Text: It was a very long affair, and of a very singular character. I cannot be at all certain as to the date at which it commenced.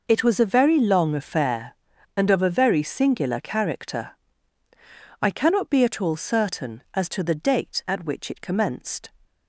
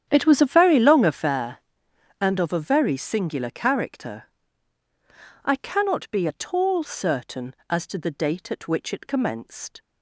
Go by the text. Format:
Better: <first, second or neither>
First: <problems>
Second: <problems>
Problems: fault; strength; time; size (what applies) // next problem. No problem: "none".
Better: first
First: none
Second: starts louder than the rest; strong; until 1.3 s; 9.5 dB